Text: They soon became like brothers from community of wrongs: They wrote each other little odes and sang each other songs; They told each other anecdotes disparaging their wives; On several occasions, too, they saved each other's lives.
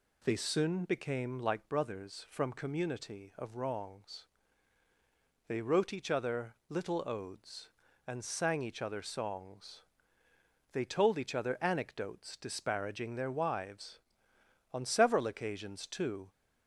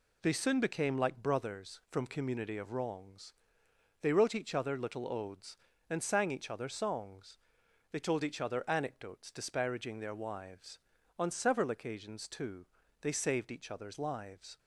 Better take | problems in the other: second | pauses between "other" and "little"; slight; at 6.5 s; 0.16 s long // stops before "they saved each other's lives"; at 16.2 s

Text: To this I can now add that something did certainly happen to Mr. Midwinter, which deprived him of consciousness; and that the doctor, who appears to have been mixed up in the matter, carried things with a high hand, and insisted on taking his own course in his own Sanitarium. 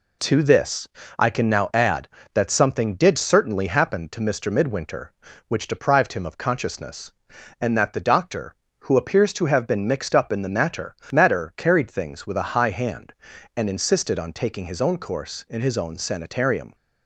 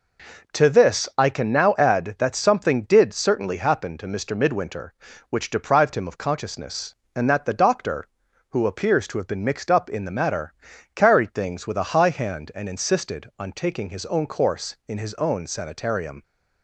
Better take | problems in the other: second | pauses between "this" and "I"; slight; at 0.8 s; 0.32 s long // says "matter" twice; at 11.1 s

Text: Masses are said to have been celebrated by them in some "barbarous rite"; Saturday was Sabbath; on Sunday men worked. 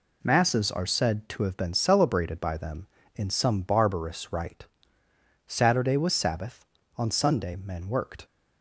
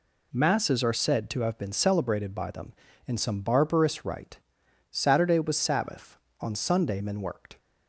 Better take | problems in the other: neither | none

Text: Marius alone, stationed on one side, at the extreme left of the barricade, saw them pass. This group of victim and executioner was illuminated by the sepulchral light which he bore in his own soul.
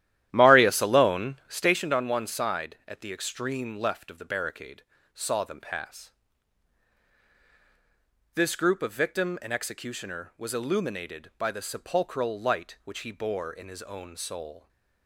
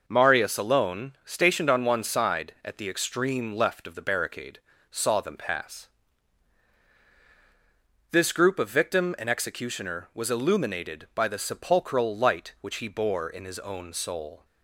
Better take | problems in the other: second | starts louder than the rest; strong; until 1.8 s; 12.5 dB

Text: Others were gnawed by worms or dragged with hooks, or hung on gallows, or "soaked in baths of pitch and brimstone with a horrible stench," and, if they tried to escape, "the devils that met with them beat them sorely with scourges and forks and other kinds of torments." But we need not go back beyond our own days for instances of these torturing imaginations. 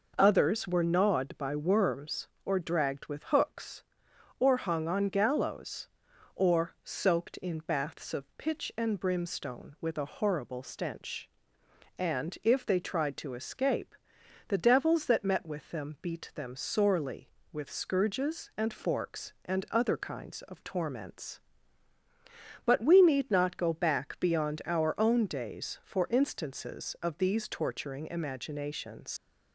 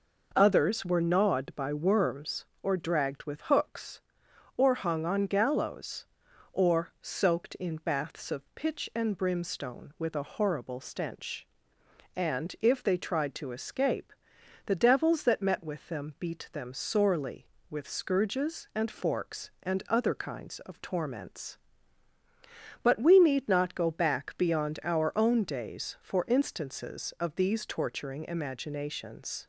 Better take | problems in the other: second | leaves "imaginations" unfinished; at 29.1 s; 115 ms

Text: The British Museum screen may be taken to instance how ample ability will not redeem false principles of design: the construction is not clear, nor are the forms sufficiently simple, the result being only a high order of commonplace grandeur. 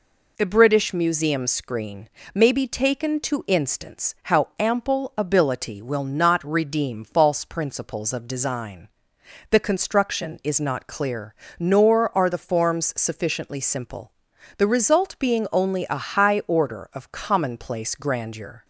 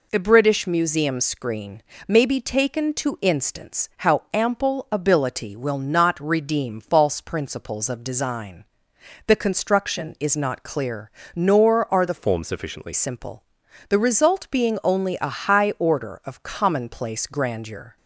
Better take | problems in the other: first | pauses between "screen" and "may"; slight; at 1.8 s; 0.24 s long; slight in the first // changes voice from "forms" to "sufficiently"; from 12.1 to 12.9 s; 0.8 s long

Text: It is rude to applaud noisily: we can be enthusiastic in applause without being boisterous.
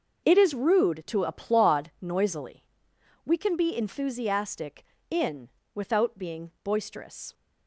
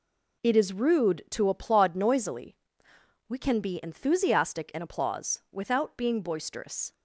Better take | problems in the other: second | starts louder than the rest; noticeable; until 1.3 s; 6 dB // skips "applause"; at 5.6 s

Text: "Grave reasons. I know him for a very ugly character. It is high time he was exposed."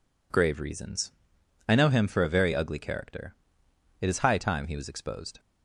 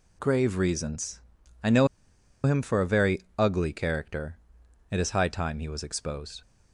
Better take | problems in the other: first | pauses between "know" and "him"; noticeable; at 1.8 s; 0.57 s long // pauses between "very" and "ugly"; slight; at 3.2 s; 0.16 s long

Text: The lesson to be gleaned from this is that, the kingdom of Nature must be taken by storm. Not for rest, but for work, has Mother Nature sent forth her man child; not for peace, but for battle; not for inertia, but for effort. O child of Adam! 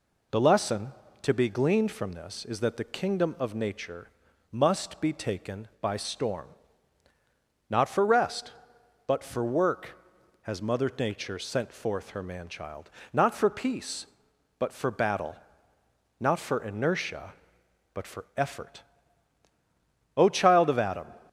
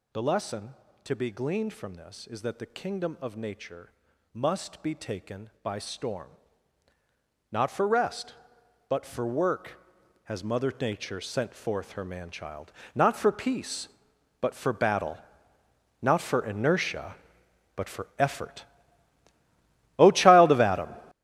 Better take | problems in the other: first | gets louder; strong; throughout; 12.5 dB // pauses between "Nature" and "must"; at 3.9 s; 0.44 s long; also in the first

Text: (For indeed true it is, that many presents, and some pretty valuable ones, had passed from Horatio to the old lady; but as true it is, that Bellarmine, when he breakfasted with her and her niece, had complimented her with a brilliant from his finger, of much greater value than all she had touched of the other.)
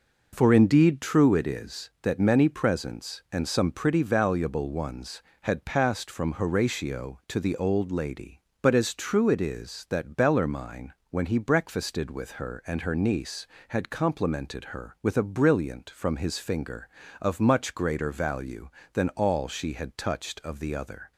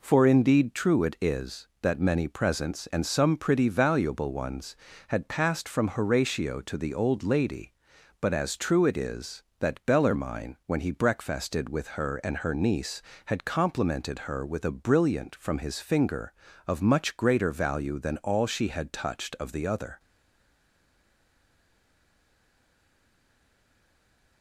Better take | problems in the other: first | stays silent after the last word; strong; from 19.9 s on; 4.5 s long

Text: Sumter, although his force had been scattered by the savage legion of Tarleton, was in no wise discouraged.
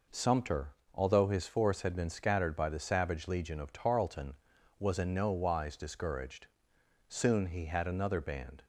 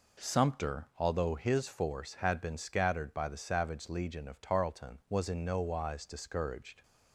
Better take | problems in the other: second | goes on to say "Soon he had another band"; from 7.0 s on; 1.5 s long

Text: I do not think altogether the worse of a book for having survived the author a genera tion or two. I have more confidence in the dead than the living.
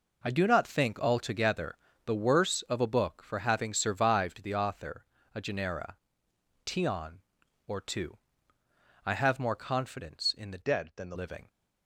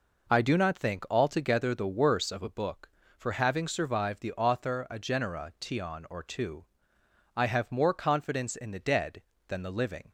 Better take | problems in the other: second | pauses between "altogether" and "the"; slight; at 1.7 s; 0.28 s long // pauses between "author" and "a"; slight; at 5.0 s; 0.28 s long // pauses between "genera" and "tion"; noticeable; at 5.9 s; 0.72 s long // changes voice from "dead" to "the"; from 10.6 to 11.1 s; 0.5 s long

